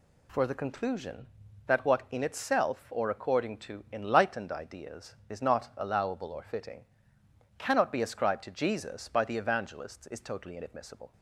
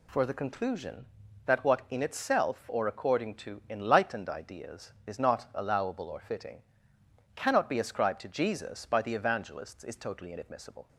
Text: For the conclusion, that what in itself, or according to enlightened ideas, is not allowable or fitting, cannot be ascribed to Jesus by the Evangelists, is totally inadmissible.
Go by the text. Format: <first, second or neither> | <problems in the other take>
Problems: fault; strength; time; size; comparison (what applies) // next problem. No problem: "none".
neither | none